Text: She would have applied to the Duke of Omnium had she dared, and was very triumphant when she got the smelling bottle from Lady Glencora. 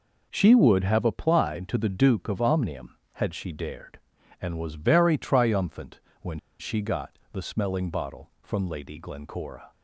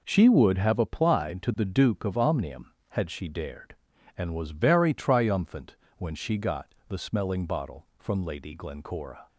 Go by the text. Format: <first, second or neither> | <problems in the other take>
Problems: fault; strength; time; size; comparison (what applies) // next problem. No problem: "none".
second | pauses between "triumphant" and "when"; slight; at 5.9 s; 0.22 s long; slight in the second // pauses between "when" and "she"; slight; at 6.3 s; 0.20 s long